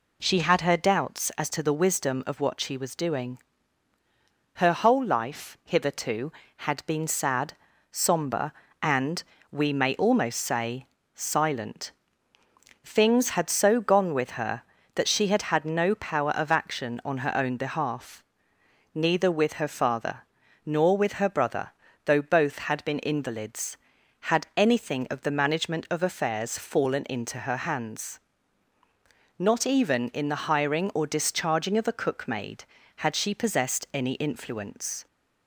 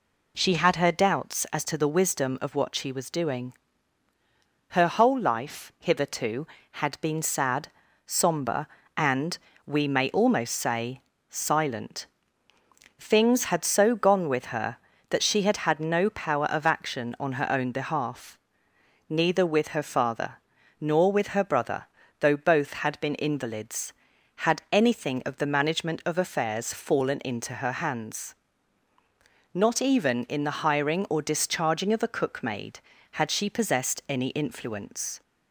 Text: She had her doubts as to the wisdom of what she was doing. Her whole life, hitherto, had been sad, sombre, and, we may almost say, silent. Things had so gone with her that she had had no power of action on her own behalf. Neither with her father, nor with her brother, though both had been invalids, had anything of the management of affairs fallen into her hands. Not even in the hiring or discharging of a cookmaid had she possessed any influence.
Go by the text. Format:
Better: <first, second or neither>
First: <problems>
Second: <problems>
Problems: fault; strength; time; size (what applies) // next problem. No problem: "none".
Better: neither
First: none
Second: none